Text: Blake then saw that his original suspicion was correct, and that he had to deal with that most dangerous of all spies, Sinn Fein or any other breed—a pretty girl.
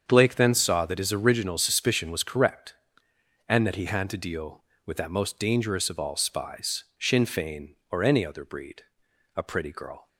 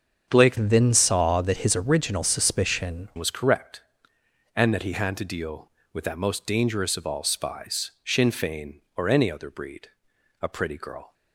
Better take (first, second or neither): first